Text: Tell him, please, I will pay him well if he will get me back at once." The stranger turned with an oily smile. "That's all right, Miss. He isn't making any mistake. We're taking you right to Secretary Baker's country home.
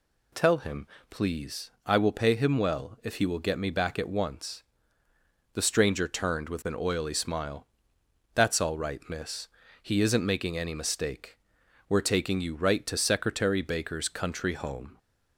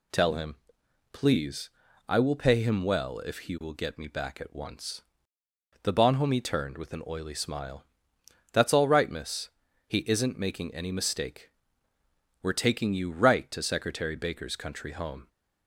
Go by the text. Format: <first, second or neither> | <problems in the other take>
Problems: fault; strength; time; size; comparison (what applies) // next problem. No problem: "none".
first | says "bonhomie" for "stranger"; at 5.9 s